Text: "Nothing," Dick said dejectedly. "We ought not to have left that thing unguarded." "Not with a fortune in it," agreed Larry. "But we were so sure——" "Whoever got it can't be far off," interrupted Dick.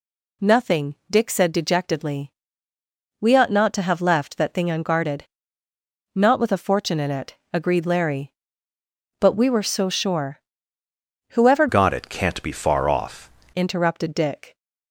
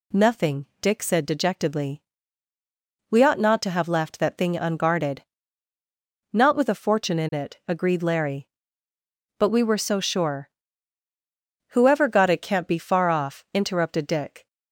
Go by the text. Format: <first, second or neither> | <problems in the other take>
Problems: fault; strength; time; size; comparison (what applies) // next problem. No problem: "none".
second | changes voice from "got" to "off"; from 11.6 to 13.2 s; 1.6 s long